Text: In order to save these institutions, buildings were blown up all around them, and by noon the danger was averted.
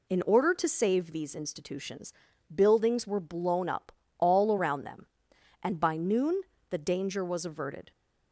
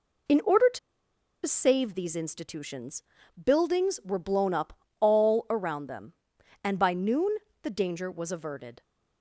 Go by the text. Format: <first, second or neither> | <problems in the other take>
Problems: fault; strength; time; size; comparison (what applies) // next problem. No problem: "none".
first | pauses between "to" and "save"; noticeable; at 0.7 s; 0.66 s long // pauses between "up" and "all"; slight; at 4.7 s; 0.28 s long; slight in the first // pauses between "noon" and "the"; slight; at 7.3 s; 0.26 s long; slight in the first